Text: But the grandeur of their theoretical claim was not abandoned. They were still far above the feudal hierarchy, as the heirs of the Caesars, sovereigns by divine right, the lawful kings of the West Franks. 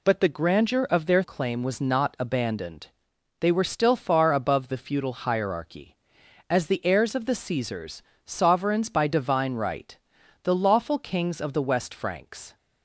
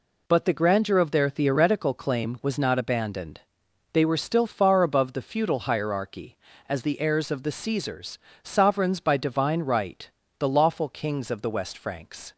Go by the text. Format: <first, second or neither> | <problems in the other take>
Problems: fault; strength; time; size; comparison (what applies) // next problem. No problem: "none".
second | skips "theoretical"; at 1.2 s